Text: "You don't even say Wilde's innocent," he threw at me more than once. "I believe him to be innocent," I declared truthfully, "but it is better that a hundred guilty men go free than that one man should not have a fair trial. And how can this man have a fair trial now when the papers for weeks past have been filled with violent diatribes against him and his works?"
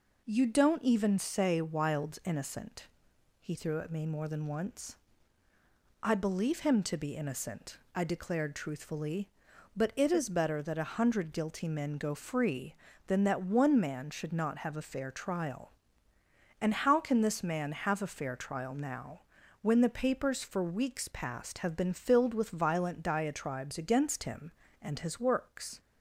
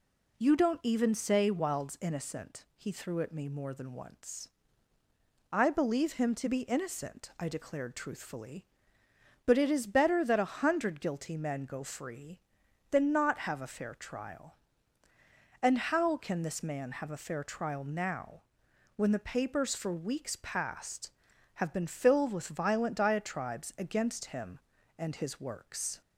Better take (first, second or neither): first